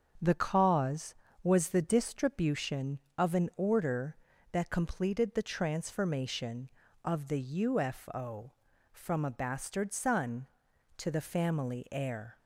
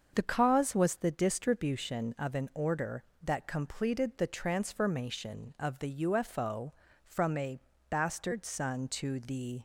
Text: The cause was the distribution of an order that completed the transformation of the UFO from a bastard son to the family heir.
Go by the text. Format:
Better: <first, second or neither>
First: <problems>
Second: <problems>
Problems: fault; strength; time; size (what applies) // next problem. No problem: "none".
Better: first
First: starts louder than the rest; until 1.4 s; 7 dB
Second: starts louder than the rest; strong; until 1.1 s; 7 dB // pauses between "a" and "bastard"; noticeable; at 7.5 s; 0.54 s long // stops before "family heir"; at 9.5 s